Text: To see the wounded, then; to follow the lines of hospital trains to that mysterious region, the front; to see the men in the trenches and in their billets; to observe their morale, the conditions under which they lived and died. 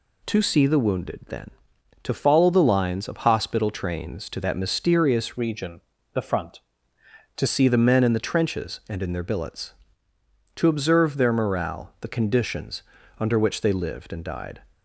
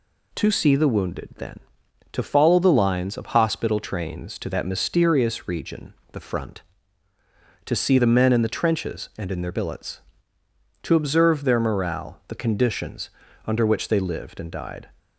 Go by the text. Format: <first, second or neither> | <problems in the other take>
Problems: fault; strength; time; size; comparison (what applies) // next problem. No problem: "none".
second | changes voice from "region" to "to"; from 5.3 to 7.4 s; 2.1 s long // pauses between "conditions" and "under"; at 12.8 s; 0.38 s long; also in the second